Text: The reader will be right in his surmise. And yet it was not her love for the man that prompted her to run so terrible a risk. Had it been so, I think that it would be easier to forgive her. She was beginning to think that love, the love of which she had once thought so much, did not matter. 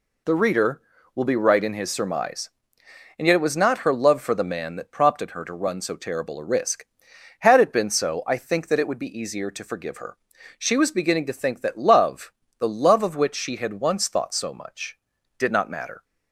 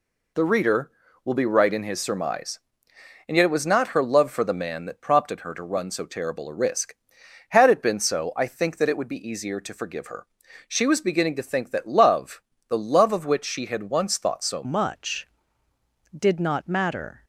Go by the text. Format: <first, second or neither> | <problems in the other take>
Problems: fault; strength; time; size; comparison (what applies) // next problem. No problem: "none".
first | changes voice at "much"; from 14.6 s on; 2.6 s long